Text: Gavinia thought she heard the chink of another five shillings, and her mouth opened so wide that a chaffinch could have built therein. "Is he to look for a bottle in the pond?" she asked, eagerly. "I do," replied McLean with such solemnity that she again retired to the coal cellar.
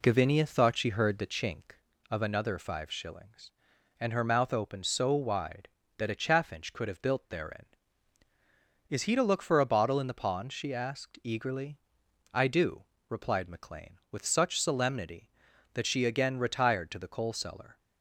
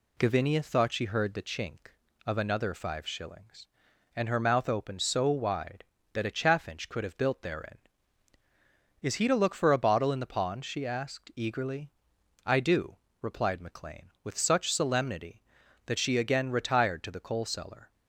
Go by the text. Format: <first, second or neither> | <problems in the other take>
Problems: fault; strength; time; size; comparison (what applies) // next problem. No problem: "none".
second | starts louder than the rest; slight; until 1.9 s; 2.5 dB